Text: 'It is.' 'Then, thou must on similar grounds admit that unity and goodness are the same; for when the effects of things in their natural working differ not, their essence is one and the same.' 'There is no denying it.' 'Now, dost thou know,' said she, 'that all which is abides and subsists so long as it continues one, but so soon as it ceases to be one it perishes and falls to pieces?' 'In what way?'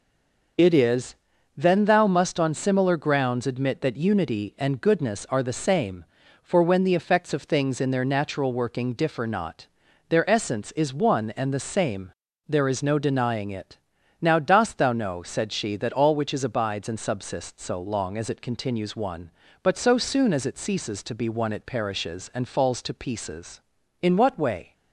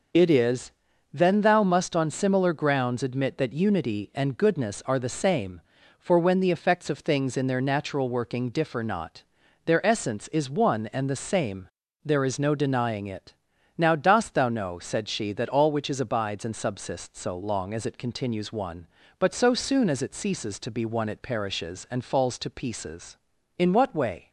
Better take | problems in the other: second | stays silent before the first word; slight; until 0.5 s; 0.5 s long

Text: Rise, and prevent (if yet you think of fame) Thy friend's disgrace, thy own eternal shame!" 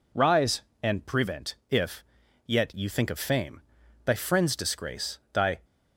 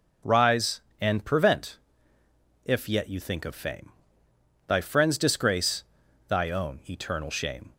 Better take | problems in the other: second | pauses between "if" and "yet"; at 2.0 s; 0.44 s long // stops before "own eternal shame"; at 5.6 s

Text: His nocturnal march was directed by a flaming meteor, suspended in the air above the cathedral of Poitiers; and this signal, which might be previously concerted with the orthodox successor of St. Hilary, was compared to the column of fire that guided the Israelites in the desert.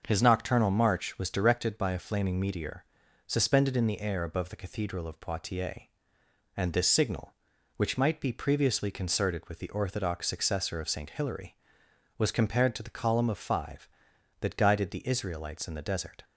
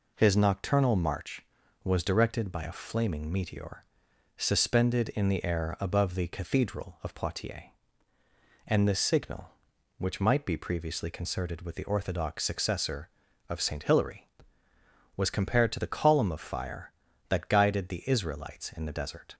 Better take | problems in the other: second | starts louder than the rest; until 1.0 s; 6.5 dB // says "five" for "fire"; at 13.3 s

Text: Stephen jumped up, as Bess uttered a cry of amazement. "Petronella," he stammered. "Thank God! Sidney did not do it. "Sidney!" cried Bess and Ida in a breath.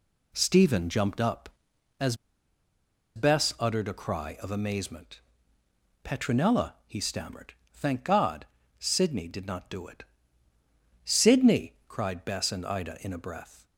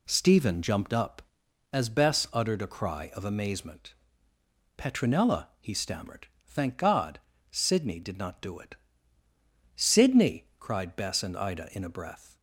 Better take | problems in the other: second | pauses between "as" and "Bess"; at 2.1 s; 0.99 s long

